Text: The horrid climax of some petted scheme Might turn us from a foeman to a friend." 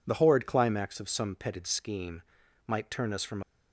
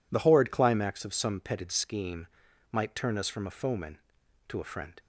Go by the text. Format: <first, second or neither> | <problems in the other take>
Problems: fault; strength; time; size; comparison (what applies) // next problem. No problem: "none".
second | pauses between "scheme" and "Might"; noticeable; at 2.2 s; 0.46 s long; noticeable in the second // stops before "a foeman to a friend"; at 3.4 s